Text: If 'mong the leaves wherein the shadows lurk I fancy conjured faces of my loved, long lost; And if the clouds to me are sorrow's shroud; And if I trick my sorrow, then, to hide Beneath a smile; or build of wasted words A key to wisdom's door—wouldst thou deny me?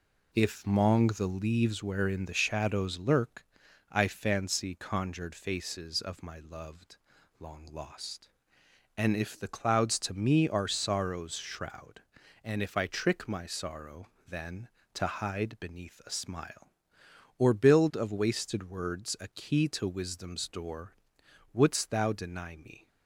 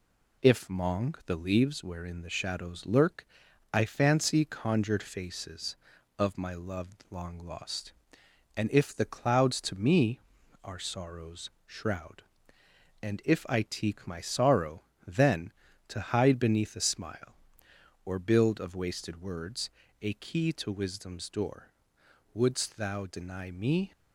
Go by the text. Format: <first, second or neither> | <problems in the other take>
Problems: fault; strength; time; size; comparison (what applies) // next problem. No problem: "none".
first | pauses between "lurk" and "I"; noticeable; at 3.2 s; 0.46 s long; noticeable in the first // pauses between "sorrow's" and "shroud"; slight; at 11.5 s; 0.16 s long // says "teak" for "trick"; at 13.6 s // pauses between "words" and "A"; slight; at 19.7 s; 0.31 s long